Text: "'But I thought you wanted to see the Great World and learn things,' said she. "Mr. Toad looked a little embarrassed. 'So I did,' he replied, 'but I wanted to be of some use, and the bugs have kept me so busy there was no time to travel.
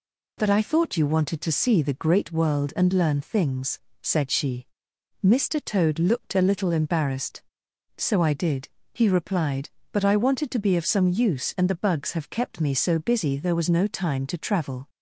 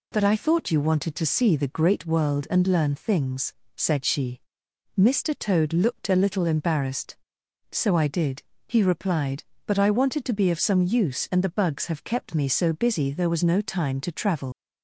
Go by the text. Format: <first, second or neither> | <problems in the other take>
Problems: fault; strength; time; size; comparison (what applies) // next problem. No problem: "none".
first | leaves "travel" unfinished; at 14.5 s; 105 ms